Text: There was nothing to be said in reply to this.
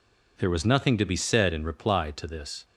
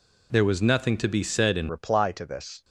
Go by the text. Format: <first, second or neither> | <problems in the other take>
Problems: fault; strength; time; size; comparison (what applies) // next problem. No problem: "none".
first | changes voice at "reply"; from 1.6 s on; 1.0 s long